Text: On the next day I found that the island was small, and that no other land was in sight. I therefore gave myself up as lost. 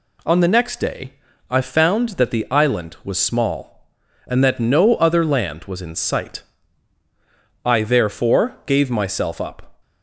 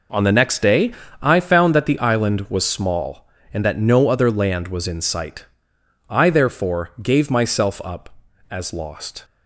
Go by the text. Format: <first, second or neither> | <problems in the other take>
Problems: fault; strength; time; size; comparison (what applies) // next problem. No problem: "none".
second | pauses between "day" and "I"; slight; at 1.1 s; 0.36 s long; slight in the second // stops before "as lost"; at 9.8 s